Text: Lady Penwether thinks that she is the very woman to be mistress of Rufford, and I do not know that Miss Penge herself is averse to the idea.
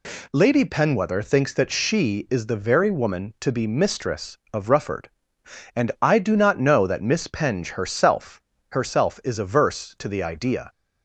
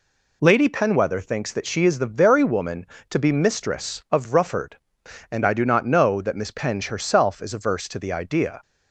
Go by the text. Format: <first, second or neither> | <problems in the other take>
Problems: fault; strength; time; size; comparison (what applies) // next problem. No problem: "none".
second | says "herself" twice; at 8.6 s